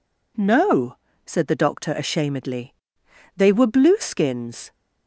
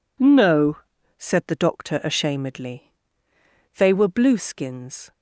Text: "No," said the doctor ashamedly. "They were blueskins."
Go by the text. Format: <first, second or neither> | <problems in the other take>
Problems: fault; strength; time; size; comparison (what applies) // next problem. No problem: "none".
neither | none